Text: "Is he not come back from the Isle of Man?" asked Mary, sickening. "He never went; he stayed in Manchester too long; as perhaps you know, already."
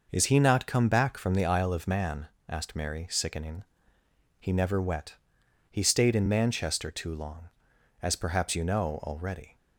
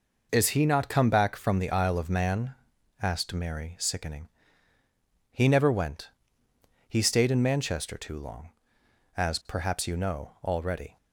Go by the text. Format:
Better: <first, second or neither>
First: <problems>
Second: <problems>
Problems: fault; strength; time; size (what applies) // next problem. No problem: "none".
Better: second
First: says "wet" for "went"; at 4.8 s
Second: none